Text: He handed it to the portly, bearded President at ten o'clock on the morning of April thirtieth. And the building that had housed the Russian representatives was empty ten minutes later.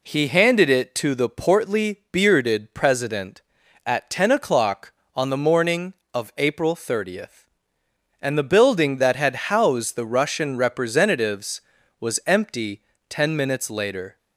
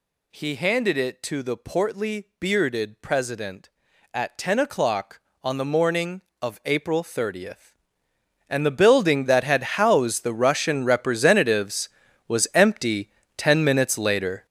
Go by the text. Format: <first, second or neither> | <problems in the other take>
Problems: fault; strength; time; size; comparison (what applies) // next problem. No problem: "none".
first | gets louder; strong; throughout; 10 dB // pauses between "empty" and "ten"; slight; at 13.0 s; 0.26 s long; slight in the first